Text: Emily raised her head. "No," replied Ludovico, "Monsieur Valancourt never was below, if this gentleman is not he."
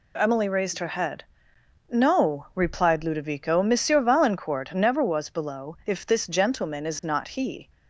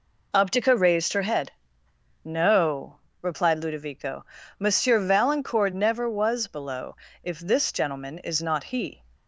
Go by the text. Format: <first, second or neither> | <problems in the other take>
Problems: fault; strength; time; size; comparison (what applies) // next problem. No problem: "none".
first | says "Optica" for "Emily"; at 0.3 s